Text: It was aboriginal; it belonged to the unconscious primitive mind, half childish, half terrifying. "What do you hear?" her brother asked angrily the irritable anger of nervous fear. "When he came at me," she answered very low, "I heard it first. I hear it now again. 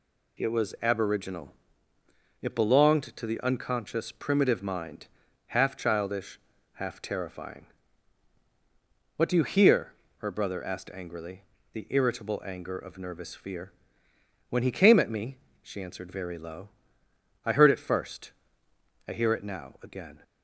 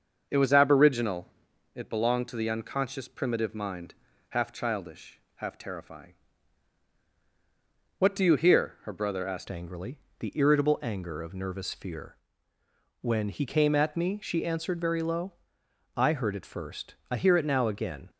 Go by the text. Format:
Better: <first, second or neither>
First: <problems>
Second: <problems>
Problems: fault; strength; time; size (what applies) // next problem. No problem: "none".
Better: first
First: pauses between "angrily" and "the"; slight; at 11.4 s; 0.30 s long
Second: starts louder than the rest; until 1.3 s; 6.5 dB // changes voice at "angrily"; from 9.4 s on; 8.6 s long // pauses between "angrily" and "the"; slight; at 9.9 s; 0.22 s long